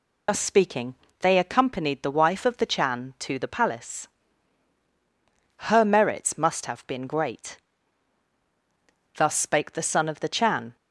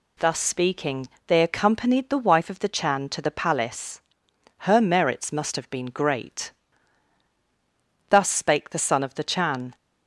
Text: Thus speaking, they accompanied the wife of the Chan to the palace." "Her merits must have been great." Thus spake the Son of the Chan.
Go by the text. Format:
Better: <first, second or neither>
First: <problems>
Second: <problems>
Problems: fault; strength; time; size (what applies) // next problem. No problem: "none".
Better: second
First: loses the start of "Thus"; at 0.2 s; 50 ms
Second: none